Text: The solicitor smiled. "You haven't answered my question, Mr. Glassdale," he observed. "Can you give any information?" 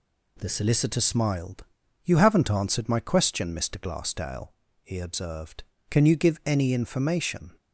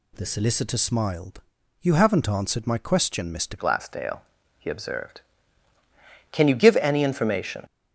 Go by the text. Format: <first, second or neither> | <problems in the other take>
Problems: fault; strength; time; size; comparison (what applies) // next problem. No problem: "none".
first | changes voice at "Glassdale"; from 3.5 s on; 4.1 s long